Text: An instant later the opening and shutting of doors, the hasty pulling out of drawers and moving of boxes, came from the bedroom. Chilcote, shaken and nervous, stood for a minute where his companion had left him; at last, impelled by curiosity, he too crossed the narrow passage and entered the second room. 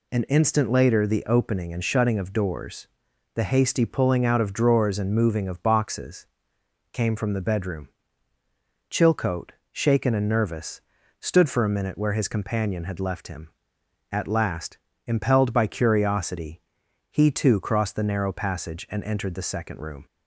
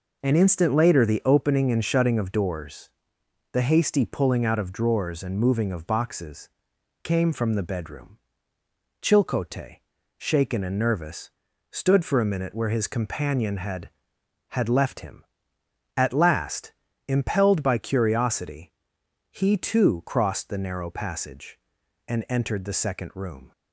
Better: first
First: none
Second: says "had" twice; at 14.4 s

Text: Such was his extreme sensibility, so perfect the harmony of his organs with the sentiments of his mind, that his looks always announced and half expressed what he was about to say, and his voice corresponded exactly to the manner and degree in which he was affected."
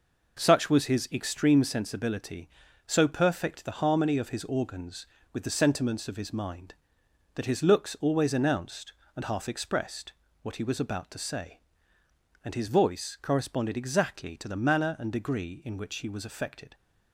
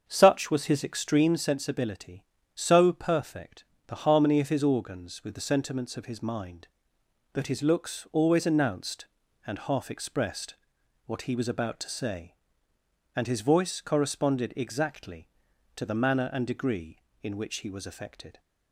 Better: first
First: pauses between "expressed" and "what"; slight; at 10.1 s; 0.30 s long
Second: starts louder than the rest; until 1.4 s; 7 dB // pauses between "perfect" and "the"; slight; at 3.6 s; 0.22 s long // pauses between "expressed" and "what"; noticeable; at 10.5 s; 0.50 s long

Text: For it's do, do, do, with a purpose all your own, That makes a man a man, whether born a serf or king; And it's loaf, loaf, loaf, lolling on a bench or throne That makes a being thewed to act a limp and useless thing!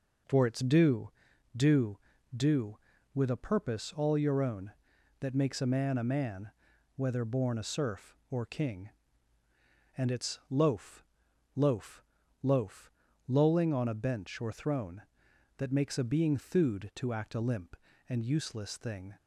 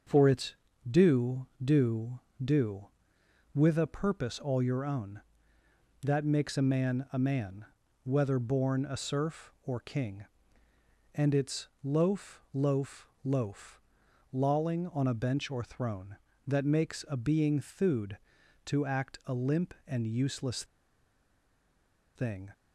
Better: first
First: none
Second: starts louder than the rest; until 1.4 s; 6.5 dB // pauses between "it's" and "loaf"; slight; at 11.6 s; 0.16 s long // pauses between "useless" and "thing"; strong; at 20.6 s; 1.5 s long

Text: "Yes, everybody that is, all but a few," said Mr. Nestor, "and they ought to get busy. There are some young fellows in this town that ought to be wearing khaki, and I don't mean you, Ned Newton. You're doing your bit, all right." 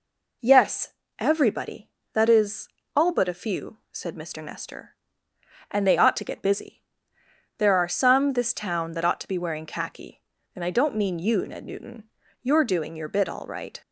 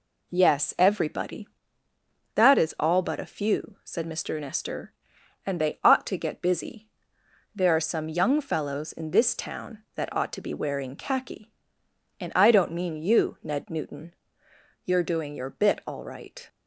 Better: second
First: skips "young fellows in"; at 8.3 s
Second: none

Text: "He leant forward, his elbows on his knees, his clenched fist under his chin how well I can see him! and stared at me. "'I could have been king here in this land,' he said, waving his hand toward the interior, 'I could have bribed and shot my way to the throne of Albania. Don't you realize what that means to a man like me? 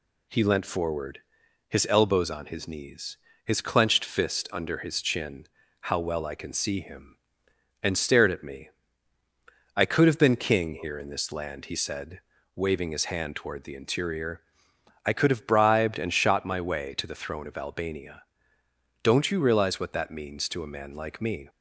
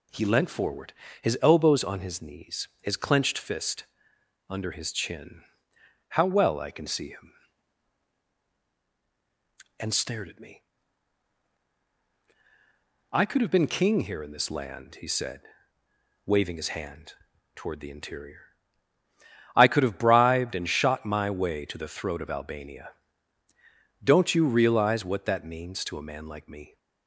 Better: first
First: pauses between "chin" and "how"; slight; at 5.4 s; 0.36 s long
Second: pauses between "fist" and "under"; noticeable; at 3.8 s; 0.64 s long // pauses between "chin" and "how"; noticeable; at 5.4 s; 0.70 s long // pauses between "hand" and "toward"; at 17.1 s; 0.40 s long // says "throat" for "throne"; at 21.8 s

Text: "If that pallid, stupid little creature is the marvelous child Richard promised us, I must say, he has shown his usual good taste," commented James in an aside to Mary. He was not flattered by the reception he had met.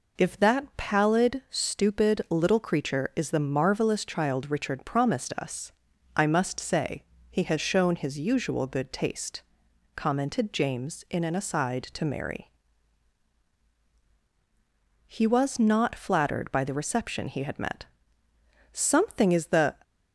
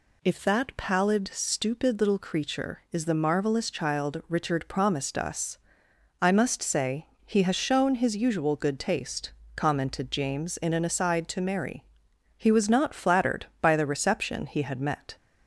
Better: second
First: goes on to say "Something is the"; noticeable; from 18.7 s on; 1.0 s long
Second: none

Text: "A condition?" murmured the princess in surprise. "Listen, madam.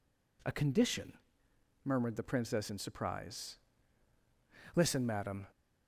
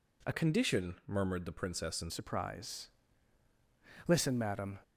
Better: first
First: none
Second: changes voice from "condition" to "in"; from 0.3 to 2.1 s; 1.8 s long

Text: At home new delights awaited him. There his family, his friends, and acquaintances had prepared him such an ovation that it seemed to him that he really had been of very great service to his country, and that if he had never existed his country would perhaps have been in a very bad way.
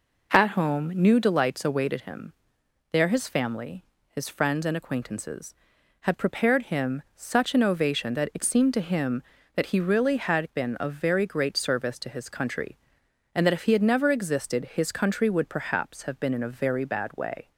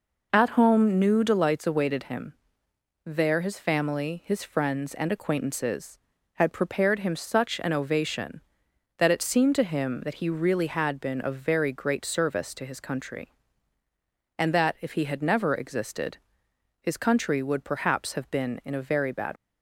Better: first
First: none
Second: pauses between "existed" and "his"; noticeable; at 16.1 s; 0.62 s long // stops before "way"; at 19.3 s

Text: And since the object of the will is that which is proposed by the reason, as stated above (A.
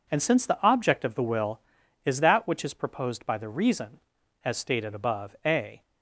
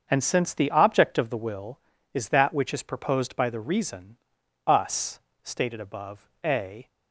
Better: first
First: none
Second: starts louder than the rest; until 1.1 s; 6.5 dB // says "us" for "as"; at 4.6 s

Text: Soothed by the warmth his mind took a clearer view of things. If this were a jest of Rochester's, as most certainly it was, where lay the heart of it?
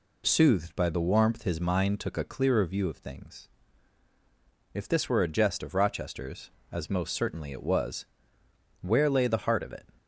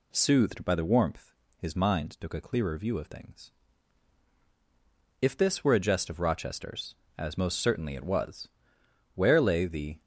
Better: first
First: none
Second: pauses between "warmth" and "his"; slight; at 1.3 s; 0.26 s long // stops before "heart of it"; at 10.0 s

